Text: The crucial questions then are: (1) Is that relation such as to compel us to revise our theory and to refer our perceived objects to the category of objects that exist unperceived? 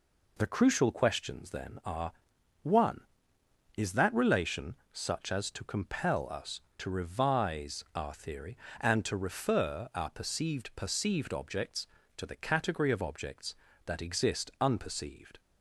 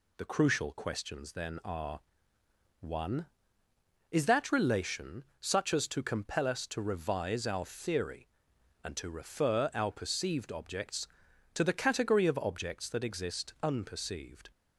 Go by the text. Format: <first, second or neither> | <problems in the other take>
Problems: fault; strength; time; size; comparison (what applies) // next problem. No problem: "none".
second | pauses between "relation" and "such"; slight; at 4.7 s; 0.16 s long; slight in the second // says "perceived" twice; at 10.7 s